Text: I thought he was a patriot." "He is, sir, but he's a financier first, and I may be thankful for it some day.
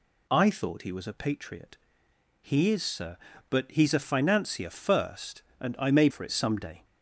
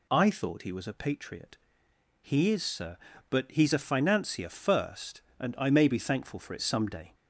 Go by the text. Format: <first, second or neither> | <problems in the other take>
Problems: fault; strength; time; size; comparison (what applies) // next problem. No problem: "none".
second | skips "be thankful"; at 6.0 s